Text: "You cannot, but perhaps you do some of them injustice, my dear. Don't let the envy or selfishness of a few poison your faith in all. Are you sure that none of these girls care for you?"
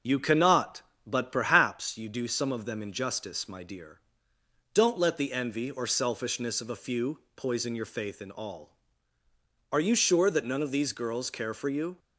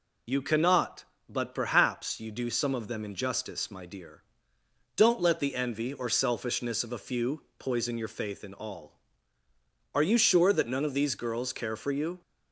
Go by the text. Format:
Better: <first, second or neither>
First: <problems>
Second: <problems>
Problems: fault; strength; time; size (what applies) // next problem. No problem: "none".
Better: second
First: starts louder than the rest; until 1.9 s; 7 dB // pauses between "few" and "poison"; slight; at 7.1 s; 0.16 s long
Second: pauses between "few" and "poison"; slight; at 7.4 s; 0.16 s long